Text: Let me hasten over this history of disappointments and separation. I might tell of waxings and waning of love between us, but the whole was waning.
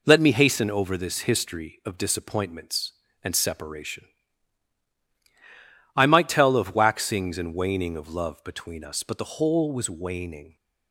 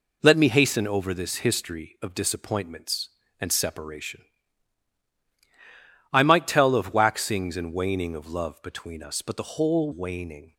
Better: first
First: none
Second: skips "was"; at 9.9 s

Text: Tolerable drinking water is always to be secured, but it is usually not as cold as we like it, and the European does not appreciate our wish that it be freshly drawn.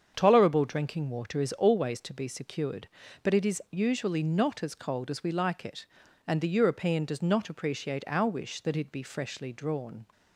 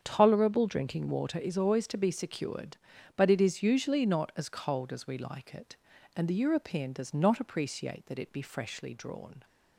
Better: first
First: starts louder than the rest; strong; until 1.1 s; 7.5 dB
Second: starts louder than the rest; strong; until 1.0 s; 8 dB // skips "our wish"; at 8.0 s

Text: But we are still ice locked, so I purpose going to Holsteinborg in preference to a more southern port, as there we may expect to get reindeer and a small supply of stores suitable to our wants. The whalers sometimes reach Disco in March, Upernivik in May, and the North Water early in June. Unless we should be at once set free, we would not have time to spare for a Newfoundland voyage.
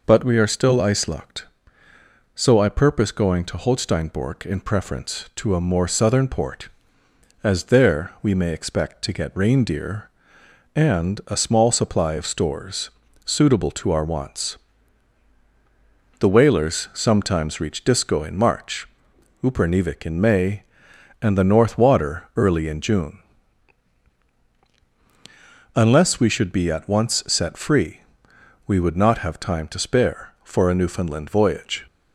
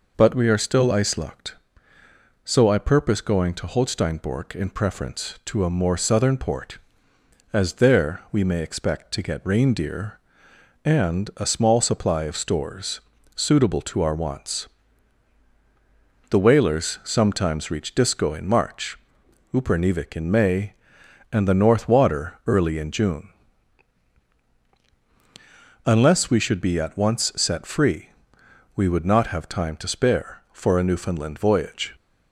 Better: neither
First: pauses between "stores" and "suitable"; slight; at 12.9 s; 0.34 s long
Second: pauses between "stores" and "suitable"; slight; at 13.0 s; 0.34 s long

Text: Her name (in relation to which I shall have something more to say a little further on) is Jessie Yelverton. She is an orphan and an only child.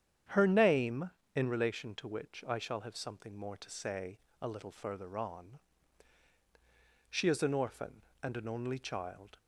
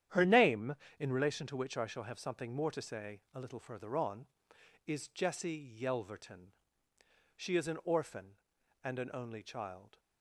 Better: second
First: starts louder than the rest; strong; until 1.5 s; 9 dB // pauses between "say" and "a"; slight; at 4.1 s; 0.22 s long // skips "is Jessie Yelverton"; at 6.3 s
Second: starts louder than the rest; strong; until 1.3 s; 10 dB

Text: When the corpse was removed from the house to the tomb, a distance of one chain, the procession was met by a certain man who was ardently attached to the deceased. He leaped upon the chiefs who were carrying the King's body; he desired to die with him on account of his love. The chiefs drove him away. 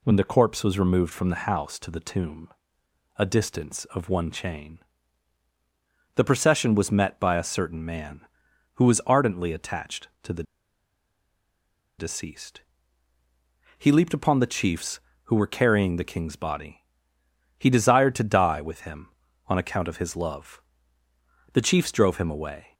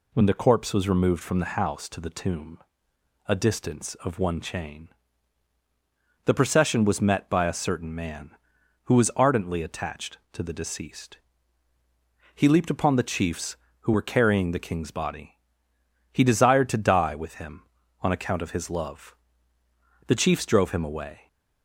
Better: second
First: pauses between "the" and "deceased"; strong; at 10.4 s; 1.5 s long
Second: none

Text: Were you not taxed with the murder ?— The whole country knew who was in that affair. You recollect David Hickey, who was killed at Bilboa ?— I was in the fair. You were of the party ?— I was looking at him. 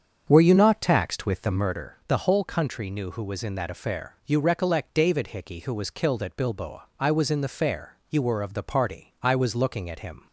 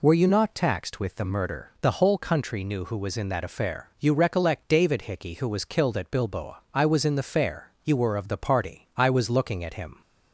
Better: second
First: starts louder than the rest; strong; until 1.7 s; 7 dB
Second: none

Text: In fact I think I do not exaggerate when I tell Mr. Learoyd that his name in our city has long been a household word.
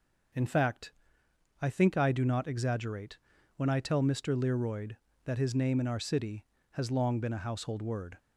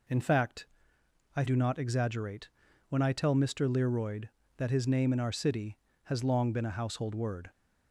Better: first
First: pauses between "fact" and "I"; noticeable; at 0.9 s; 0.70 s long // pauses between "exaggerate" and "when"; at 3.1 s; 0.38 s long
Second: pauses between "fact" and "I"; noticeable; at 0.6 s; 0.70 s long // skips "think I"; at 1.4 s // pauses between "exaggerate" and "when"; at 2.4 s; 0.40 s long

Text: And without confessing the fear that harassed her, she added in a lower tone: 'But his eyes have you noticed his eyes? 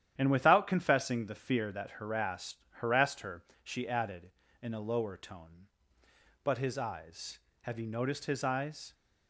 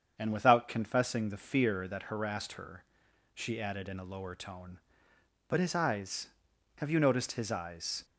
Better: second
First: starts louder than the rest; strong; until 1.1 s; 10.5 dB // says "harassed" twice; at 2.7 s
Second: starts louder than the rest; strong; until 1.1 s; 7.5 dB

